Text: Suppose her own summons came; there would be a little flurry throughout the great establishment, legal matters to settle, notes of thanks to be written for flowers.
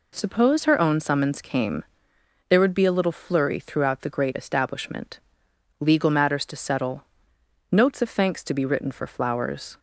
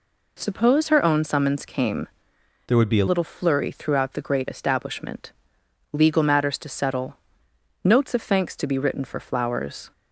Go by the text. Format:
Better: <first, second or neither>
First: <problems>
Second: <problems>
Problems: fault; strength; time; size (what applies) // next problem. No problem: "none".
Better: first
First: none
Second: changes voice from "there" to "a"; from 2.6 to 3.0 s; 0.4 s long